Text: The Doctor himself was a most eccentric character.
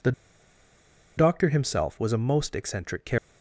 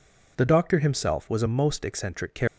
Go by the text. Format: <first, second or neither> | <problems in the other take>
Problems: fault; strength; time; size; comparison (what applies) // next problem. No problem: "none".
second | pauses between "The" and "Doctor"; at 0.1 s; 1.0 s long